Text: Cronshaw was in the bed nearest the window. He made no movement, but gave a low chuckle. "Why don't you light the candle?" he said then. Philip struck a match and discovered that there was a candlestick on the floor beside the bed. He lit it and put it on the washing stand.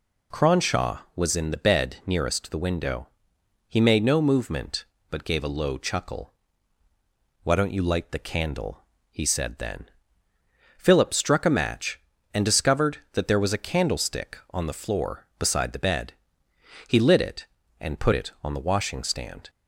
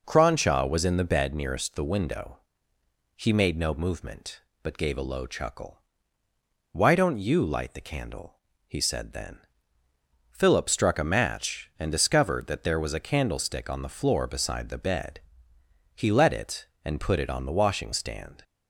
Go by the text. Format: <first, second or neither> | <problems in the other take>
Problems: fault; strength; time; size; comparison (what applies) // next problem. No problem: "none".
first | says "let" for "lit"; at 16.1 s